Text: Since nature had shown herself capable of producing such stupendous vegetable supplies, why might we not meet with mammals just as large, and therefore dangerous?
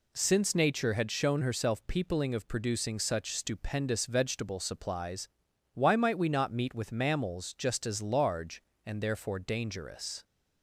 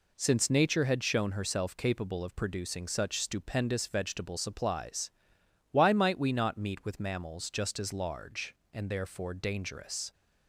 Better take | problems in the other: second | says "peopling" for "capable"; at 1.8 s

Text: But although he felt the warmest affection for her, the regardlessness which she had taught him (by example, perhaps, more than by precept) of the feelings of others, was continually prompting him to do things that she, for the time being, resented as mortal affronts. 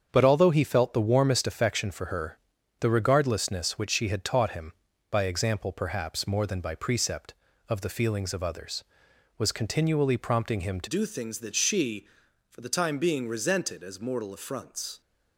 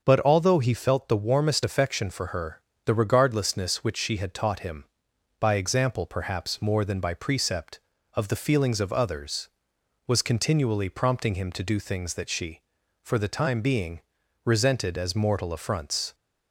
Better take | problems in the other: second | starts louder than the rest; strong; until 1.1 s; 7.5 dB; also in the second // changes voice at "do"; from 10.8 s on; 4.2 s long

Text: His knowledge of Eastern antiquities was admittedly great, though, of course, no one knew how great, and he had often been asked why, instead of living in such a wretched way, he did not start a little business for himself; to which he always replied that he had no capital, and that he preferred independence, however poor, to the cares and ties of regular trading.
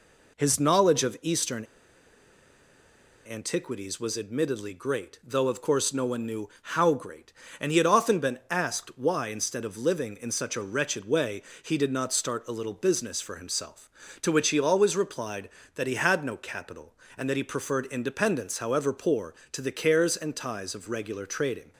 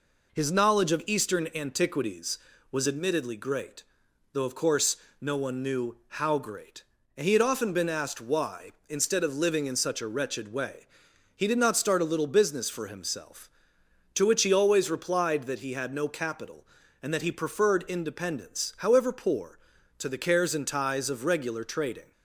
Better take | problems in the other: second | pauses between "Eastern" and "antiquities"; strong; at 1.6 s; 1.6 s long

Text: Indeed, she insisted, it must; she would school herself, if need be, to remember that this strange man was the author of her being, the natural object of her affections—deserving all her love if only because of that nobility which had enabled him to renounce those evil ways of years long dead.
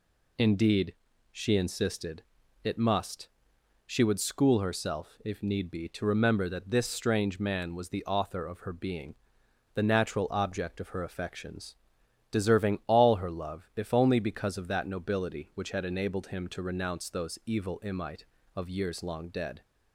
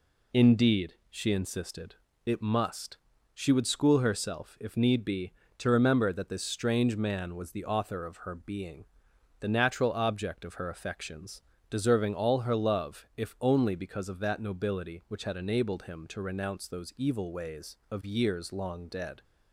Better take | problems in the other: second | says "imite" for "ways"; at 17.8 s

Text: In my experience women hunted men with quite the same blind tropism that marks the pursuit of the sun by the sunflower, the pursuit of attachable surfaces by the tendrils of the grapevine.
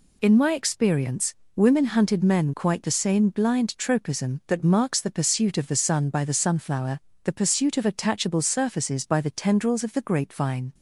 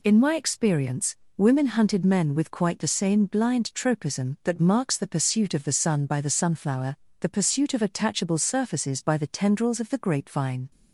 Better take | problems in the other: second | pauses between "experience" and "women"; slight; at 1.3 s; 0.22 s long; slight in the second // skips "with"; at 2.5 s

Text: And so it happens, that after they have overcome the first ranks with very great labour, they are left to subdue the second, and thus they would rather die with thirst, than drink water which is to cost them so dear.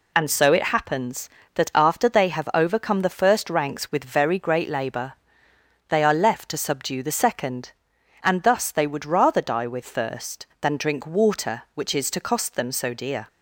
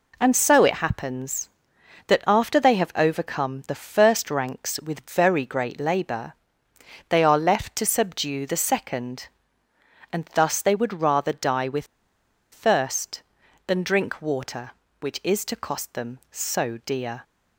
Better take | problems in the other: first | pauses between "with" and "thirst"; noticeable; at 11.8 s; 0.67 s long

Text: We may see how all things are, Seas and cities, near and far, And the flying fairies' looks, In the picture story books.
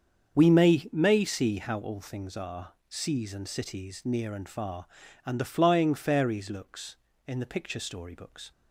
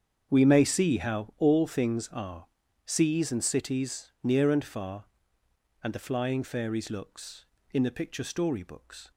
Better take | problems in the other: second | starts louder than the rest; until 1.3 s; 7 dB; strong in the second // says "may" twice; at 0.9 s

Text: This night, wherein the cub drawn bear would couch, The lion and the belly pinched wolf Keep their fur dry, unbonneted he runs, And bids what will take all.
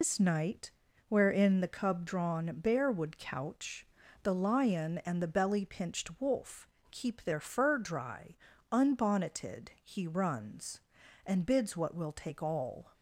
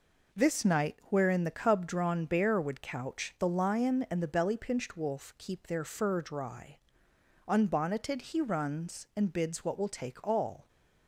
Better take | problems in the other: second | loses the start of "This"; at 0.0 s; 135 ms // pauses between "wolf" and "Keep"; slight; at 6.6 s; 0.22 s long

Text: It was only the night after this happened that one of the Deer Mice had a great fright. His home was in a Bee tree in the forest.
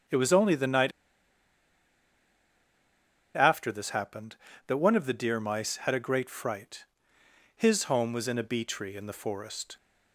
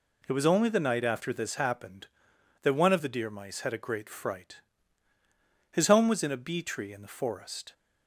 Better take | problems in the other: second | starts louder than the rest; strong; until 3.5 s; 8.5 dB // pauses between "night" and "after"; strong; at 0.9 s; 2.4 s long

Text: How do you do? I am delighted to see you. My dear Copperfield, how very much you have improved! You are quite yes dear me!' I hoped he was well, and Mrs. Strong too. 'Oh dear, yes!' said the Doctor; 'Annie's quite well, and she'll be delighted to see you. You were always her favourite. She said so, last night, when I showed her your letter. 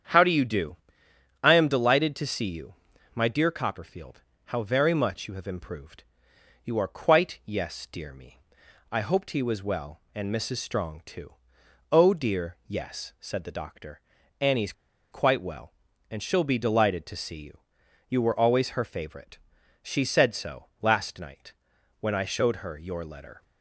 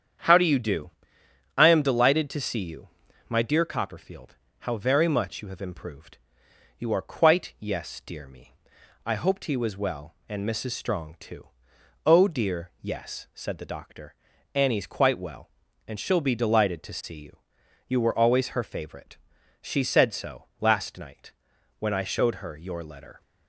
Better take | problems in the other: second | starts louder than the rest; strong; until 1.7 s; 8.5 dB; strong in the second // pauses between "Annie's" and "quite"; at 14.7 s; 0.40 s long

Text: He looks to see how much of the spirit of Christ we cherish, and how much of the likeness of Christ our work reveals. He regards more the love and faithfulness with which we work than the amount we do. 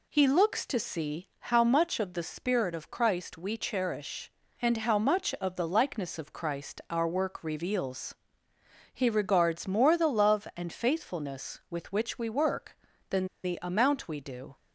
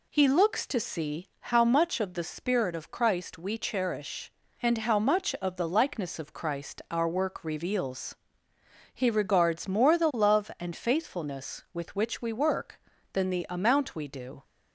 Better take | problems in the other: second | pauses between "than" and "the"; slight; at 13.2 s; 0.18 s long

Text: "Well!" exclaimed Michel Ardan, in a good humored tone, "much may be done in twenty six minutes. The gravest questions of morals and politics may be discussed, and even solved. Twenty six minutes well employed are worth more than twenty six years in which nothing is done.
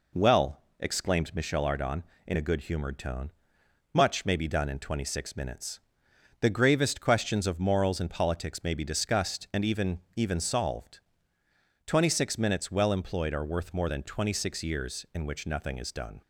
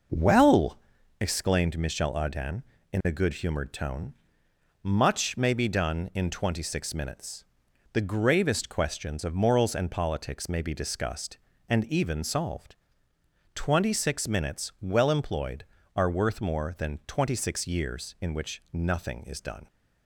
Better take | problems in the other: second | says "even" twice; at 10.1 s

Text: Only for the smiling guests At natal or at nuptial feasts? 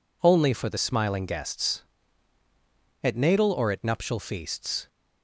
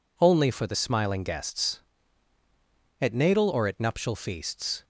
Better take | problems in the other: neither | none

